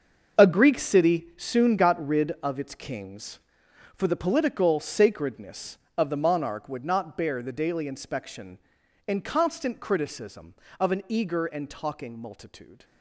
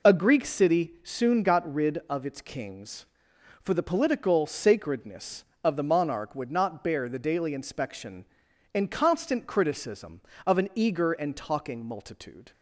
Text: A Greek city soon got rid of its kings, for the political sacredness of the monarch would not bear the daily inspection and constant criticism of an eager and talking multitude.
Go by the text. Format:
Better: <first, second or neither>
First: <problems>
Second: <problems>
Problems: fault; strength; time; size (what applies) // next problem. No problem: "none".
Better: second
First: gets quieter; strong; throughout; 12 dB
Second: none